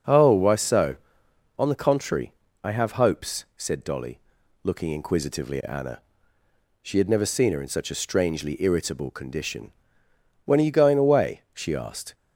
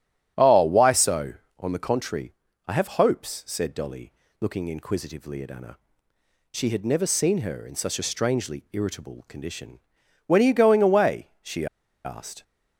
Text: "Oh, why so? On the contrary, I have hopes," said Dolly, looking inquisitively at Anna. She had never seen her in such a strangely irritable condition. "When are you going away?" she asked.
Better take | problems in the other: first | starts louder than the rest; strong; until 1.6 s; 10 dB; also in the first // pauses between "she" and "asked"; at 11.6 s; 0.38 s long

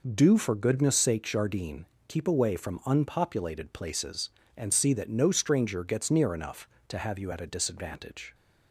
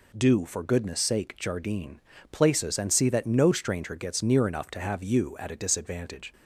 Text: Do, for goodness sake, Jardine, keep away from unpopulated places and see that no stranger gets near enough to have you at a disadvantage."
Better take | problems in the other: first | skips "keep away from unpopulated"; at 2.1 s

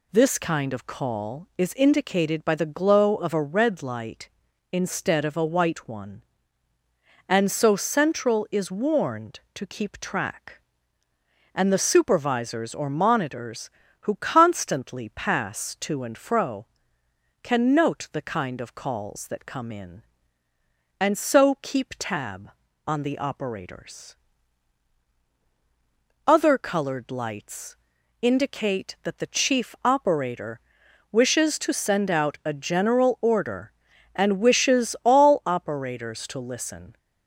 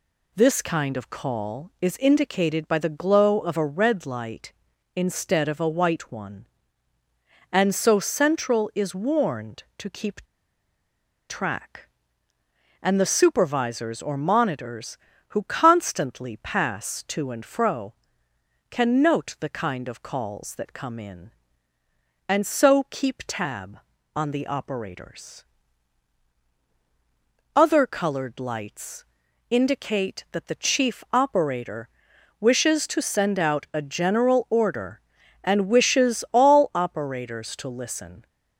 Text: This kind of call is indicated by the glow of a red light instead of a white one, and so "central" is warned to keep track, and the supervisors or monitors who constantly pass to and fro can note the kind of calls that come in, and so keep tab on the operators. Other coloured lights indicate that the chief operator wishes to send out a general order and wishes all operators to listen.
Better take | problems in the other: first | pauses between "keep" and "track"; at 10.2 s; 1.0 s long // pauses between "lights" and "indicate"; at 29.0 s; 0.44 s long; also in the first // pauses between "operator" and "wishes"; noticeable; at 31.8 s; 0.54 s long; noticeable in the first

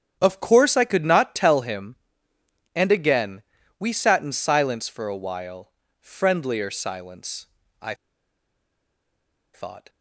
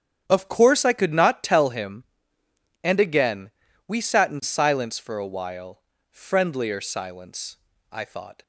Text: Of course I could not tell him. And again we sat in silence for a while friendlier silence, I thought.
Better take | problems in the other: second | starts louder than the rest; strong; until 1.2 s; 8.5 dB; strong in the second // pauses between "again" and "we"; at 3.4 s; 0.38 s long; also in the second // pauses between "while" and "friendlier"; slight; at 5.6 s; 0.30 s long; slight in the second // pauses between "I" and "thought"; strong; at 7.9 s; 1.5 s long

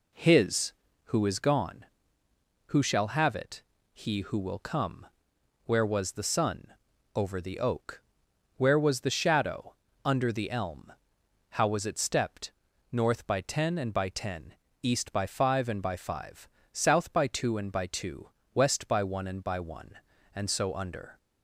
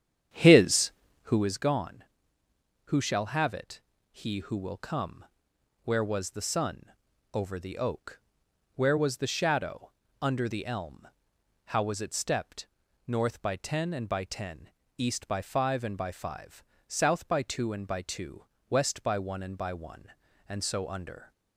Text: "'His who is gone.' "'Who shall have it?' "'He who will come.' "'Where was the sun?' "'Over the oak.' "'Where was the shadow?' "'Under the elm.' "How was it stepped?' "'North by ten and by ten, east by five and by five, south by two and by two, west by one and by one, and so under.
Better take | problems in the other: first | starts louder than the rest; strong; until 1.5 s; 9 dB

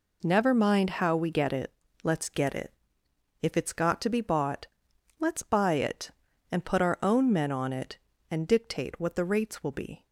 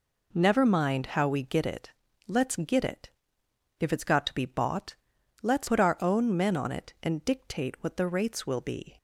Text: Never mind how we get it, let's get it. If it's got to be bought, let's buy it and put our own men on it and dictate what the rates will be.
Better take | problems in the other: first | skips "buy it and"; at 5.6 s

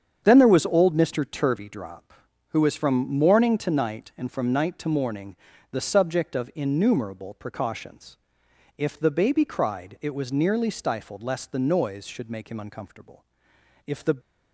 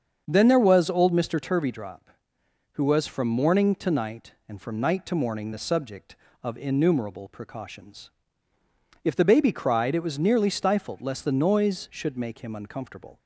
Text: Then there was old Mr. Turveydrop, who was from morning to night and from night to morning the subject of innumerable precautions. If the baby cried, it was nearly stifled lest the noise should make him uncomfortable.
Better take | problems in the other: second | starts louder than the rest; strong; until 1.2 s; 7.5 dB; also in the second // pauses between "morning" and "the"; at 5.3 s; 0.38 s long // goes on to say "If the"; slight; from 13.8 s on; 0.30 s long

